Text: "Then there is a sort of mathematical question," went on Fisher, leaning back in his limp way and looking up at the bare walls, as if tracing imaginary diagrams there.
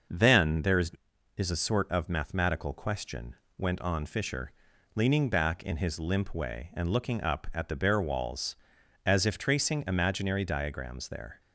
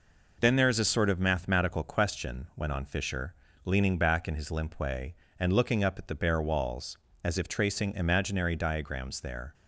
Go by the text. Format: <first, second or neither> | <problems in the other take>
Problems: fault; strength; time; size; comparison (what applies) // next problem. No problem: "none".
second | starts louder than the rest; noticeable; until 1.5 s; 6 dB // says "is" twice; at 1.3 s